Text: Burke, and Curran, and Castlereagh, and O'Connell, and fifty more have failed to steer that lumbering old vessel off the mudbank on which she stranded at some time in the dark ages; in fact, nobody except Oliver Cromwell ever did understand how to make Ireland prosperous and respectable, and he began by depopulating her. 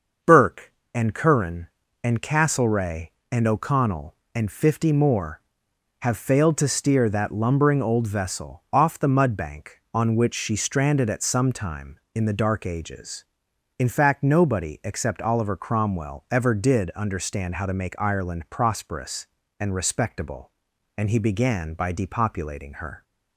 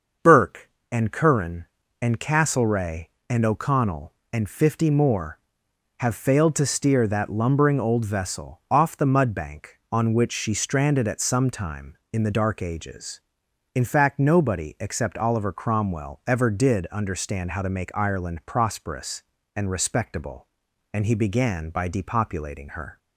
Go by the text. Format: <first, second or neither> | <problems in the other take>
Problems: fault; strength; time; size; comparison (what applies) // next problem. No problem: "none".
neither | starts louder than the rest; the same in both